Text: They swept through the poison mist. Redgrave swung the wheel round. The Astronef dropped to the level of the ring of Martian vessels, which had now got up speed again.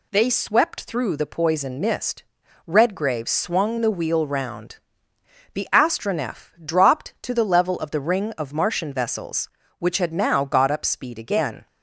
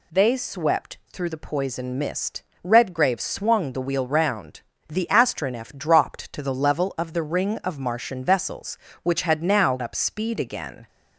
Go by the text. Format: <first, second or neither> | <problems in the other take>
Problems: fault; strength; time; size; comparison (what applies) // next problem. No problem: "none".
first | skips "got"; at 9.8 s